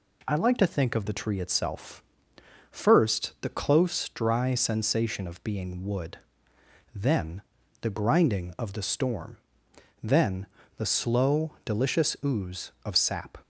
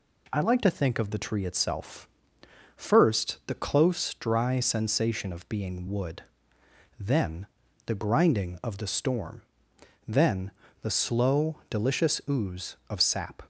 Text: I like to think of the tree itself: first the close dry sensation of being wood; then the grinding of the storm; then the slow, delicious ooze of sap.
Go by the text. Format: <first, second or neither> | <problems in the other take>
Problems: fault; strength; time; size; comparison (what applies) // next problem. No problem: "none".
neither | pauses between "then" and "the"; the same in both // pauses between "then" and "the"; slight; the same in both